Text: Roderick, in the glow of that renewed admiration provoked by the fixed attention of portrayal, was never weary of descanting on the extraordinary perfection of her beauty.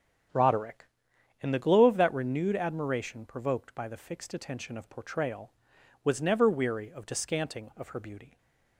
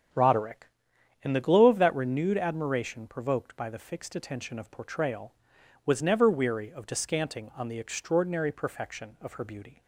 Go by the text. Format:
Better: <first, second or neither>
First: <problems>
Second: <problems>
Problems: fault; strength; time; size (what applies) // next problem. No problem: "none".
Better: second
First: starts louder than the rest; strong; until 1.9 s; 8.5 dB // skips "on the extraordinary perfection"; at 7.7 s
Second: starts louder than the rest; strong; until 1.7 s; 8.5 dB